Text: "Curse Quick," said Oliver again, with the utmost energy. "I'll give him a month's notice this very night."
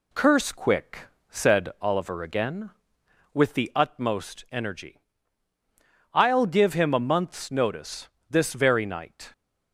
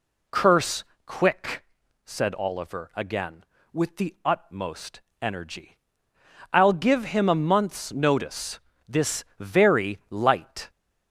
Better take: first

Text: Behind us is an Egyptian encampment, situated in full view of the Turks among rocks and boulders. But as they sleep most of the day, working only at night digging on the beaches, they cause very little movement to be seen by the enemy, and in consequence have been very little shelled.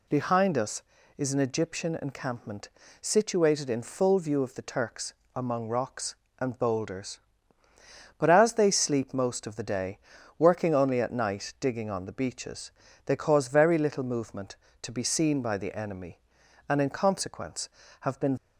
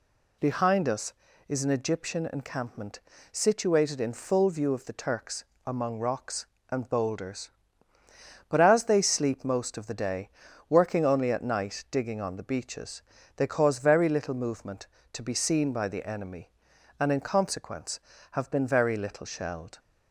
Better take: second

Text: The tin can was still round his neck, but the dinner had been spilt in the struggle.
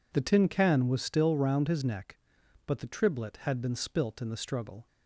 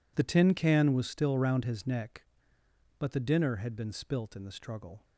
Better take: second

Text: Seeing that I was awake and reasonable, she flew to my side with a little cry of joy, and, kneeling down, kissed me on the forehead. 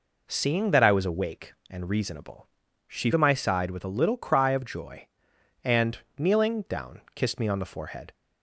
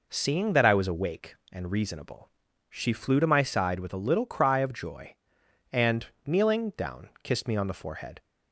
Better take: second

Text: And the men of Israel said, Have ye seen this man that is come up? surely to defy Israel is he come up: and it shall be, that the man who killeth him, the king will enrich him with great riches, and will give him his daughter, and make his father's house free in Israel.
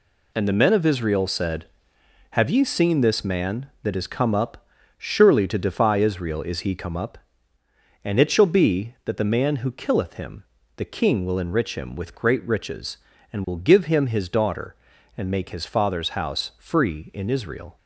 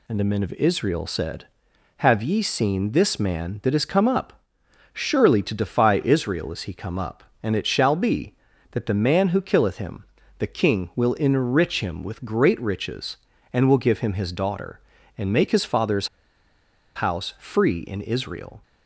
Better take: first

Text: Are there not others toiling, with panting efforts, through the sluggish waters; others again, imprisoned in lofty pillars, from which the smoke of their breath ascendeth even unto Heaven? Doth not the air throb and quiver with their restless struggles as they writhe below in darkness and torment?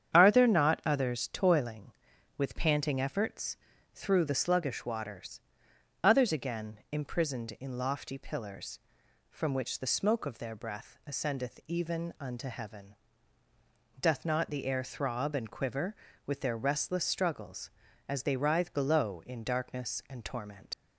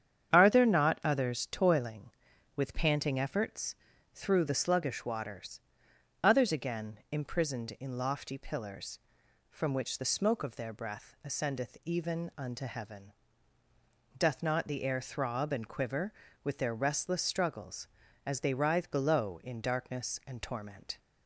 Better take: second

